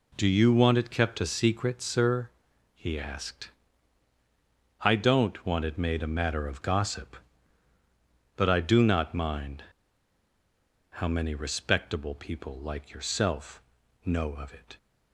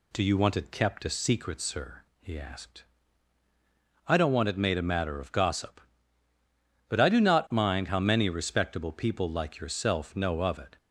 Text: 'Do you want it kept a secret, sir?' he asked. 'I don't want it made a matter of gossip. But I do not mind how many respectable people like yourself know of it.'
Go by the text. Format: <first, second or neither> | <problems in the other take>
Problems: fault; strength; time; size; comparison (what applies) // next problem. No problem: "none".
second | pauses between "mind" and "how"; strong; at 9.6 s; 1.3 s long // pauses between "yourself" and "know"; at 13.6 s; 0.42 s long